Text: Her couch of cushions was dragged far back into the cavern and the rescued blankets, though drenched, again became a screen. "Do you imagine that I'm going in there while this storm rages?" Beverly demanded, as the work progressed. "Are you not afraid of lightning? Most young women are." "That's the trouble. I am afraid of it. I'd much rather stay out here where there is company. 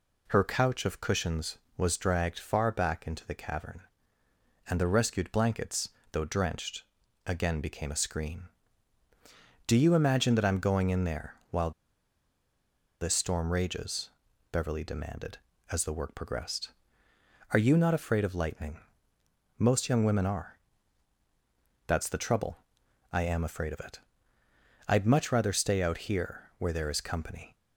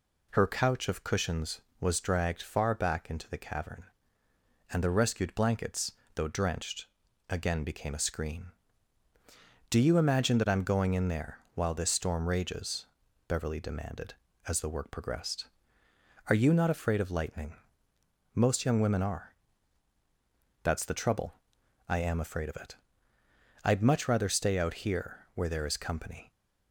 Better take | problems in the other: second | pauses between "there" and "while"; slight; at 11.3 s; 0.16 s long; slight in the second // pauses between "while" and "this"; strong; at 11.7 s; 1.3 s long

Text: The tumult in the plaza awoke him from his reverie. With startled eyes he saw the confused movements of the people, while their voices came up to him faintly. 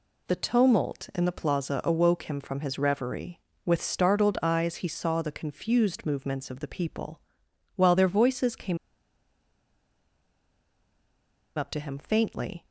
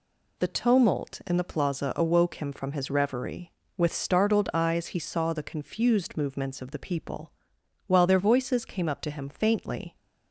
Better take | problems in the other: second | pauses between "came" and "up"; strong; at 8.7 s; 2.7 s long

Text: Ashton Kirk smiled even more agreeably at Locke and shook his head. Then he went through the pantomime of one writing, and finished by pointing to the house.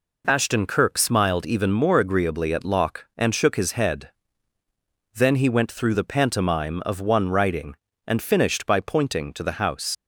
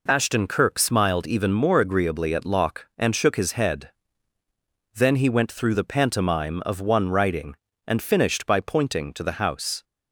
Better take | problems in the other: second | leaves "house" unfinished; at 9.9 s; 90 ms

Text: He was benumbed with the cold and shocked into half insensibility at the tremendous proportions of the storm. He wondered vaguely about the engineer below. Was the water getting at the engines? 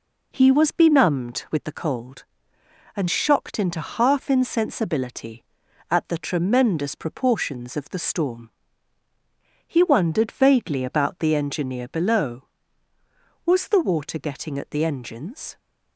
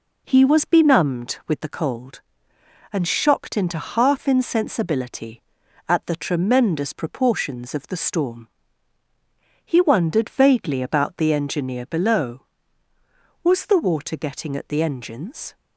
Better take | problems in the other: neither | none

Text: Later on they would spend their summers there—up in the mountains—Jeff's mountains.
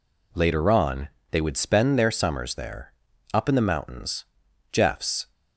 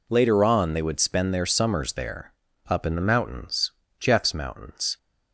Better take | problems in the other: second | pauses between "on" and "they"; slight; at 1.0 s; 0.24 s long // stops before "mountains"; at 5.3 s

